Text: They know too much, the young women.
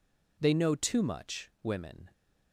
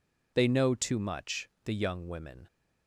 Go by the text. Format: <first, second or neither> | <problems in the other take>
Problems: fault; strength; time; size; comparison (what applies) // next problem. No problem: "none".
second | skips "the young"; at 1.5 s